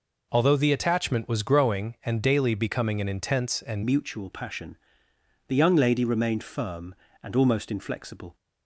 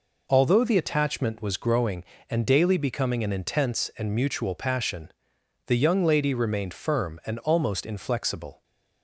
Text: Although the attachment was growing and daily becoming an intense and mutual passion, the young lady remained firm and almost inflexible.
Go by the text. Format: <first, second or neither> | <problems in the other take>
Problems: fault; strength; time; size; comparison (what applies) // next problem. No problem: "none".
second | changes voice at "mutual"; from 3.8 s on; 4.5 s long